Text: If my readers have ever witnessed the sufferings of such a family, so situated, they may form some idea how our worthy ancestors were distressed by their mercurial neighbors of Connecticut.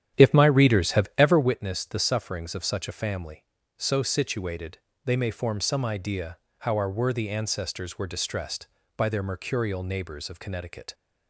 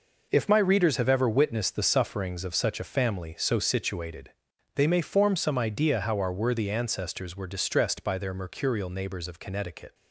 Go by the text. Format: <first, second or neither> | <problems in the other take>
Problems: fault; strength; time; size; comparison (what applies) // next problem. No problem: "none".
second | starts louder than the rest; strong; until 1.5 s; 10.5 dB // pauses between "idea" and "how"; slight; at 6.3 s; 0.22 s long